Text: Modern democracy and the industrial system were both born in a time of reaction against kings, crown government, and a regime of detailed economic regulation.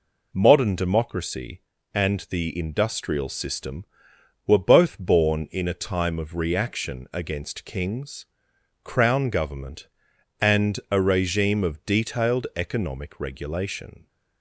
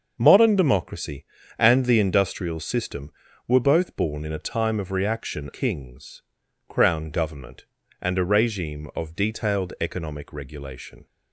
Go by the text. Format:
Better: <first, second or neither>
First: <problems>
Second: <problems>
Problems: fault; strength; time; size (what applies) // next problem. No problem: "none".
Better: first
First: none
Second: starts louder than the rest; until 1.2 s; 6 dB // skips "against"; at 5.5 s